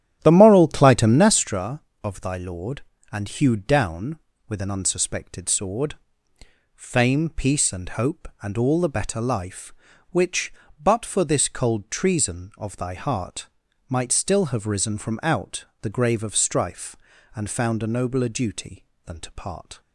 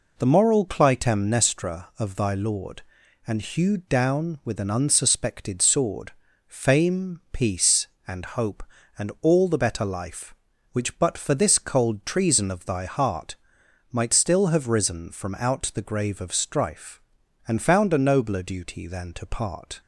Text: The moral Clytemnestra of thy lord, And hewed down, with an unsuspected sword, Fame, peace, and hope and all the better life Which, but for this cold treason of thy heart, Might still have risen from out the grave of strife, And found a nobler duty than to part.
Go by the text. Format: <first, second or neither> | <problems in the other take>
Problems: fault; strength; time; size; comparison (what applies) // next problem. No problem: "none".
second | starts louder than the rest; strong; until 1.4 s; 11 dB // pauses between "out" and "the"; slight; at 15.6 s; 0.16 s long